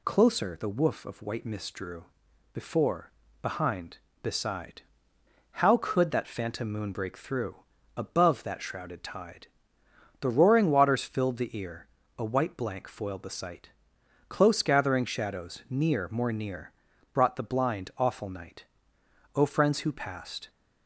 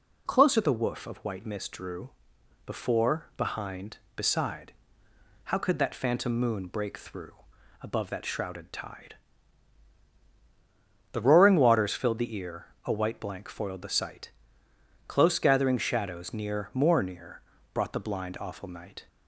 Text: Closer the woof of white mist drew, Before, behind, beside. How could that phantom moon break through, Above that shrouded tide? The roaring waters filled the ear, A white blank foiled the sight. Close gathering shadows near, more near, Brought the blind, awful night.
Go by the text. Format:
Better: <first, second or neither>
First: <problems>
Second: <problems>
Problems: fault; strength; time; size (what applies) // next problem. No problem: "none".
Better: second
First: goes on to say "O friends who passed"; noticeable; from 19.3 s on; 1.1 s long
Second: none